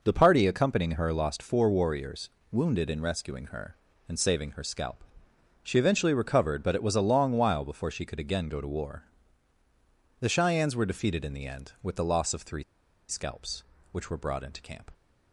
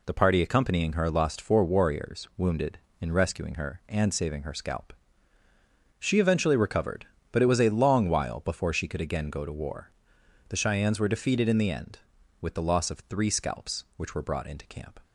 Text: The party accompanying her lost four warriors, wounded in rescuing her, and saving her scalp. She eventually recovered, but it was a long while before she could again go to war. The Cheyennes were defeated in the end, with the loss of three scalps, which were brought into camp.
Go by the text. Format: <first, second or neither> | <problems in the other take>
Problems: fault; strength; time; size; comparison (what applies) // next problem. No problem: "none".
second | pauses between "three" and "scalps"; at 12.6 s; 0.45 s long